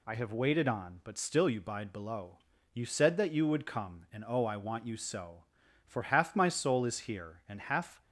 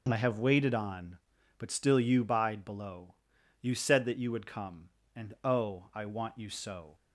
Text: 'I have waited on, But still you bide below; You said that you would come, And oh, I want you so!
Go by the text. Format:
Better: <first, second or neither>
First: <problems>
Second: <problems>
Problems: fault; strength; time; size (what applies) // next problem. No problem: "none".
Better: second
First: goes on to say "For half my soul is here And half"; strong; from 5.8 s on; 2.1 s long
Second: none